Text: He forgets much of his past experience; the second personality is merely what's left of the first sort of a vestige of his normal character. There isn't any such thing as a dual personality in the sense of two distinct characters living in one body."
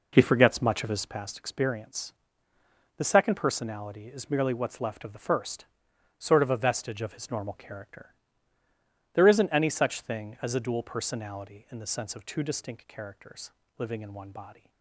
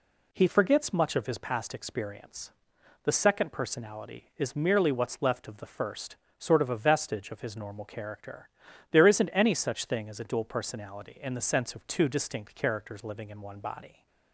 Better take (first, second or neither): second